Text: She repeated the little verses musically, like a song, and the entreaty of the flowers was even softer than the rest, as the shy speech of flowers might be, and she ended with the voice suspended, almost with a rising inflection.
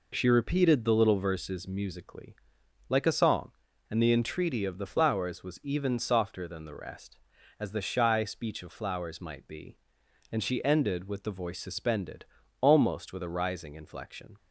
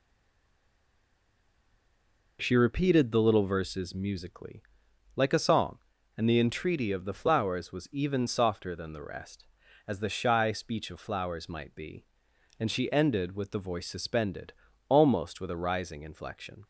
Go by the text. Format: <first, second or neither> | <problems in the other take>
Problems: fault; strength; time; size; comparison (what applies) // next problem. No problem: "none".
first | stays silent before the first word; until 2.3 s; 2.3 s long